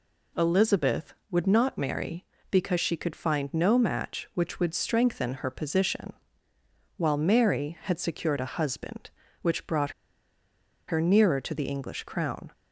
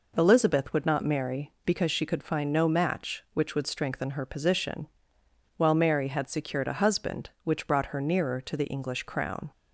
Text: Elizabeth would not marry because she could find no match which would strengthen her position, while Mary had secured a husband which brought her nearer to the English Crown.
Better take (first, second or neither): second